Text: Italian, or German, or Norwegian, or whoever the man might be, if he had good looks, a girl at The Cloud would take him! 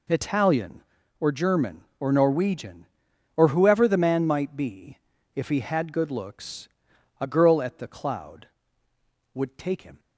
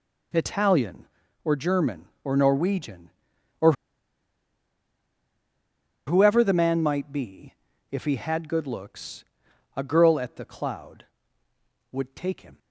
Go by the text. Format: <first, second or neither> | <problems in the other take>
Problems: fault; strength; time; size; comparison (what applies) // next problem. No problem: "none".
first | pauses between "or" and "whoever"; strong; at 3.7 s; 2.3 s long